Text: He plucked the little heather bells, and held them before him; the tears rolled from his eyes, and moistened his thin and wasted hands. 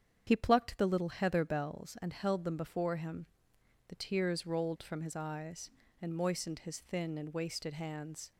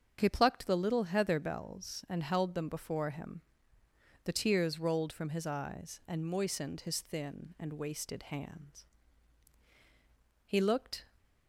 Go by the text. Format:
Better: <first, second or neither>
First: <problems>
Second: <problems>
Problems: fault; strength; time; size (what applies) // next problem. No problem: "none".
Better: first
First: starts louder than the rest; strong; until 1.2 s; 8 dB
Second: starts louder than the rest; strong; until 1.2 s; 7.5 dB // goes on to say "He looked"; noticeable; from 10.4 s on; 0.62 s long